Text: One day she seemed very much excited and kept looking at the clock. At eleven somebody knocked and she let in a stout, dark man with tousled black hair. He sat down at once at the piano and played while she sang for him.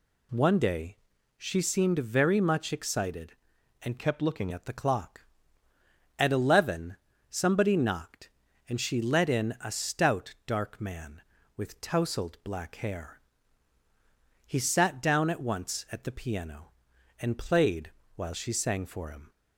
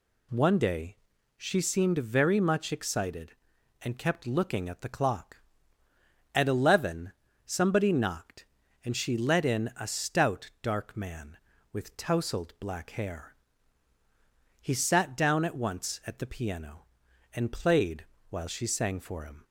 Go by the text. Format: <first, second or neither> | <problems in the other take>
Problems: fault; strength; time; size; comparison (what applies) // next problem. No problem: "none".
second | pauses between "day" and "she"; at 0.9 s; 0.42 s long; also in the second // changes voice from "kept" to "looking"; from 3.9 to 4.4 s; 0.5 s long // pauses between "eleven" and "somebody"; slight; at 6.9 s; 0.34 s long; slight in the second // pauses between "played" and "while"; slight; at 17.8 s; 0.26 s long; slight in the second